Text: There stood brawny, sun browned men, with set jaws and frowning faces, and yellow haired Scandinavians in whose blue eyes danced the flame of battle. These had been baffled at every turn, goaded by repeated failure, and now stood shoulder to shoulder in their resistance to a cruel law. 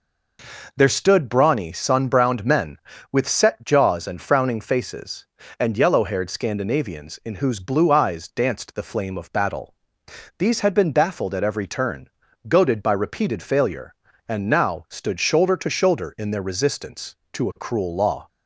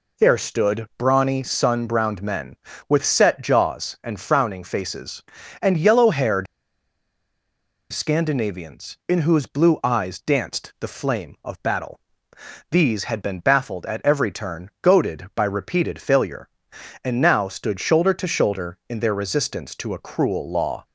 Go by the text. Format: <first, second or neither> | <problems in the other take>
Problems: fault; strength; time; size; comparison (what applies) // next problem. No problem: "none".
first | pauses between "haired" and "Scandinavians"; strong; at 6.4 s; 1.4 s long